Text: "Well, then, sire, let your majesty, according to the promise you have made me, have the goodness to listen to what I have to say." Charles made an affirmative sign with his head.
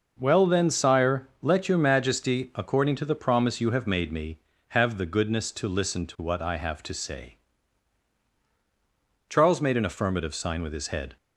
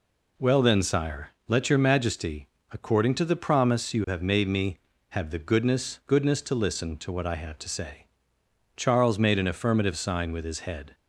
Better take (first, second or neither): first